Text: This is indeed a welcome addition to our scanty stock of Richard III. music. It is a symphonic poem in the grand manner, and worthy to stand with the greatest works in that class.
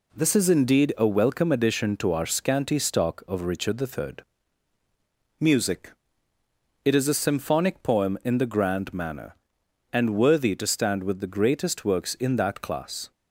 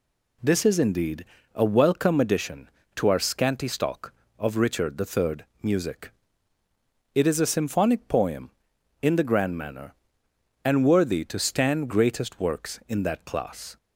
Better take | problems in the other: first | pauses between "indeed" and "a"; slight; at 1.2 s; 0.28 s long // skips "with the"; at 11.9 s

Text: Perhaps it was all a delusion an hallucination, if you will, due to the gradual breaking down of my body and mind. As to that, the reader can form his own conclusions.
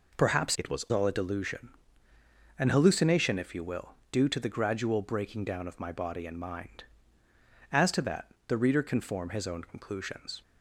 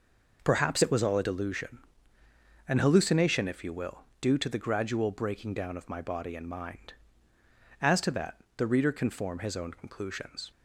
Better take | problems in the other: second | changes voice from "it" to "was"; from 0.5 to 0.8 s; 0.3 s long // pauses between "delusion" and "an"; noticeable; at 1.6 s; 0.90 s long; noticeable in the second

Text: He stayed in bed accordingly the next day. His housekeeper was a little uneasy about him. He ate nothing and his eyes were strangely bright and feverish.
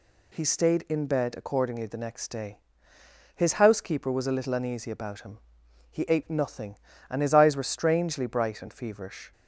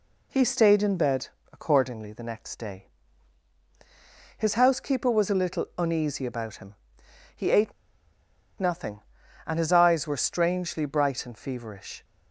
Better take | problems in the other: first | pauses between "bed" and "accordingly"; slight; at 1.2 s; 0.26 s long // pauses between "ate" and "nothing"; noticeable; at 7.7 s; 0.87 s long

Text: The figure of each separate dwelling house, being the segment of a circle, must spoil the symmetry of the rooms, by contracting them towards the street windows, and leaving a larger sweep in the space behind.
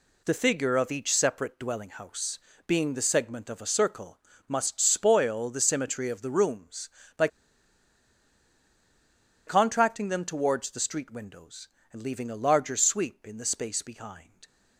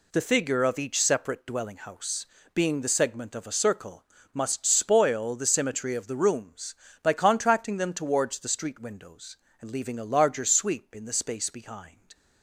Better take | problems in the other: second | pauses between "by" and "contracting"; strong; at 7.2 s; 2.1 s long

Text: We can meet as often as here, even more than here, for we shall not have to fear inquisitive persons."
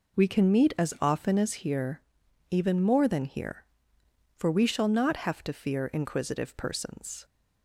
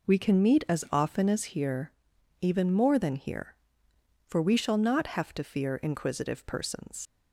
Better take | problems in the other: first | leaves "persons" unfinished; at 7.0 s; 90 ms

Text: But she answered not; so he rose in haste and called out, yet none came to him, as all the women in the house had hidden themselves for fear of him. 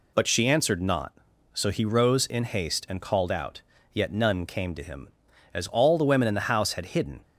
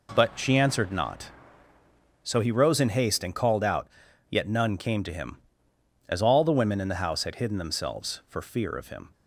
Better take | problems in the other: second | stops before "themselves for fear of him"; at 7.2 s

